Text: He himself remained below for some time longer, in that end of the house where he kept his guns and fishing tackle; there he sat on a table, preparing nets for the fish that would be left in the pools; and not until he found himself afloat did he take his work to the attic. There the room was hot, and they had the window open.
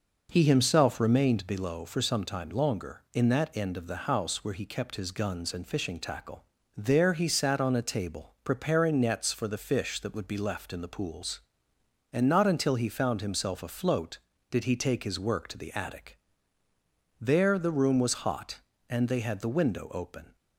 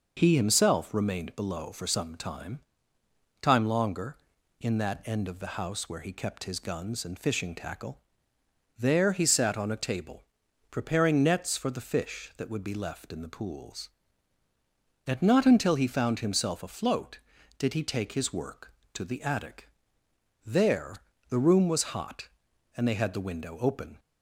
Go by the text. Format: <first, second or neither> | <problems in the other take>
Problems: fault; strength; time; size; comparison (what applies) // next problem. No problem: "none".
first | says "time" twice; at 3.3 s // pauses between "There" and "the"; slight; at 20.9 s; 0.34 s long